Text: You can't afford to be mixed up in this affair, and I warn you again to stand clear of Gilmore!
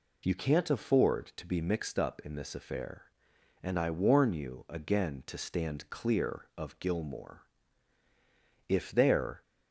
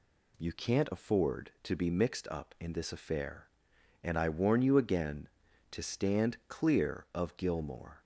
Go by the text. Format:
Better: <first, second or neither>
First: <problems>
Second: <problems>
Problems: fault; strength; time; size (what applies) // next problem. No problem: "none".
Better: second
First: goes on to say "If there"; noticeable; from 8.7 s on; 0.72 s long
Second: none